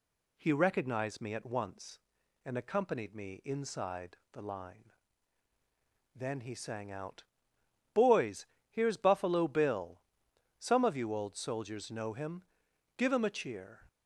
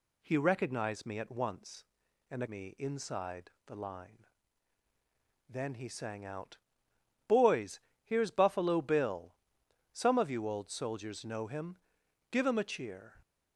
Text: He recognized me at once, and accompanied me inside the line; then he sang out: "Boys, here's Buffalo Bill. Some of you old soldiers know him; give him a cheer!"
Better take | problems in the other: first | skips "accompanied"; at 2.4 s // pauses between "inside" and "the"; slight; at 3.5 s; 0.16 s long; slight in the first

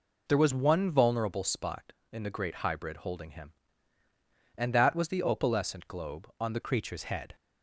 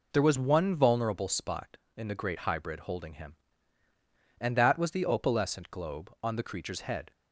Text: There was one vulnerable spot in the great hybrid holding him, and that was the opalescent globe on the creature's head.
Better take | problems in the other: second | changes voice at "creature's"; from 6.6 s on; 0.7 s long

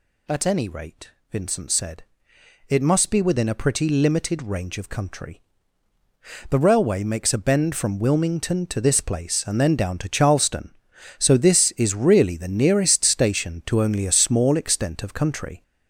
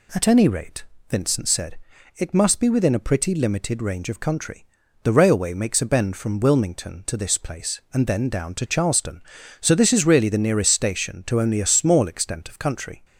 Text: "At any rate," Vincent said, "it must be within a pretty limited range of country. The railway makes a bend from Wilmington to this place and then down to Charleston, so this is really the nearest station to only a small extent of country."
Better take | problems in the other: second | gets louder; noticeable; throughout; 5 dB

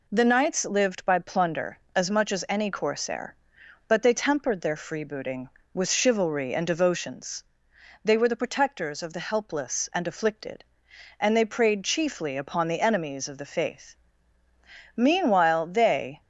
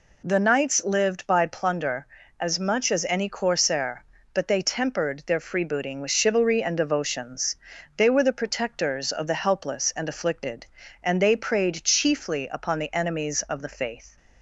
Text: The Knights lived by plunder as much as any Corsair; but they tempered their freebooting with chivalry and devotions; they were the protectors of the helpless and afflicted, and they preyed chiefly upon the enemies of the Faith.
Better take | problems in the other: second | goes on to say "Meanwhile they"; noticeable; from 14.9 s on; 1.2 s long

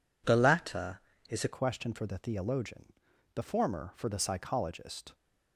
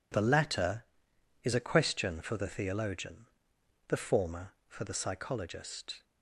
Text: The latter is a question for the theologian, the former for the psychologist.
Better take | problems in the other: second | changes voice at "question"; from 1.5 s on; 3.6 s long

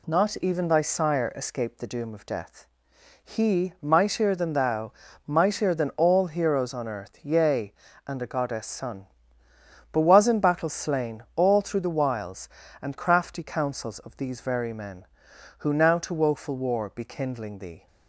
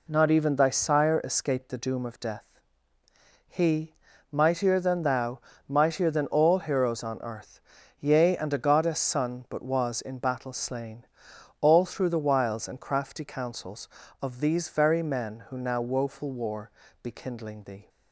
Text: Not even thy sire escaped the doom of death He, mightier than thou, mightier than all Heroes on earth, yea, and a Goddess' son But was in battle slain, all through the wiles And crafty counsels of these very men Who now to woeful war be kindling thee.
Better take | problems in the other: first | pauses between "death" and "He"; at 2.4 s; 1.0 s long; noticeable in the first // skips "to"; at 15.8 s // pauses between "war" and "be"; slight; at 16.7 s; 0.32 s long

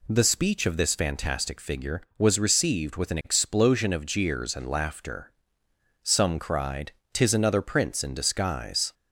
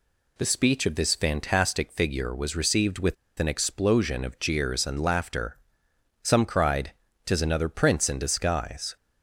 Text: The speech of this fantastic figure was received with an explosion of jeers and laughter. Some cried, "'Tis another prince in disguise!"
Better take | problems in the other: first | pauses between "with" and "an"; slight; at 3.1 s; 0.24 s long

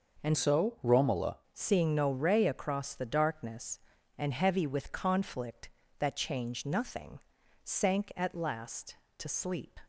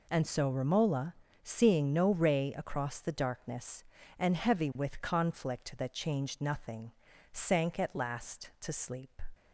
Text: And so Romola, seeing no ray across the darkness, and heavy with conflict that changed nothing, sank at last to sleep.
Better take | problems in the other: second | changes voice from "so" to "Romola"; from 0.3 to 1.3 s; 1.0 s long

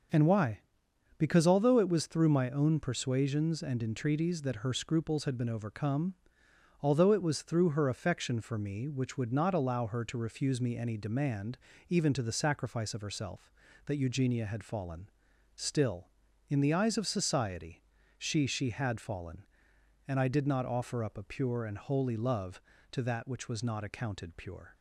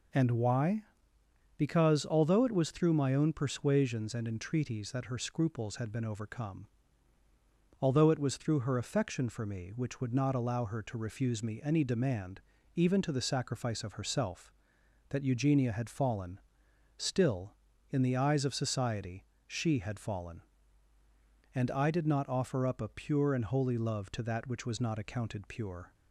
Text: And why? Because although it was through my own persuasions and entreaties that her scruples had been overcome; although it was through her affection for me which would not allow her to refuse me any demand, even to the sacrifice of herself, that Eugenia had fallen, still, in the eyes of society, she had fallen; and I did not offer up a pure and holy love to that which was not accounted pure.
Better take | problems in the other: second | starts louder than the rest; until 1.7 s; 6.5 dB // says "she" twice; at 18.4 s

